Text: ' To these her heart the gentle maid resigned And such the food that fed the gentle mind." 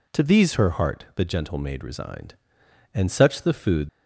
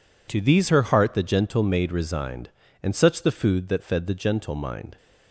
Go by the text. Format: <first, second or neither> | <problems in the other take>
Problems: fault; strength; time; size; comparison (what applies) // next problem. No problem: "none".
second | stops before "that fed the gentle mind"; at 3.8 s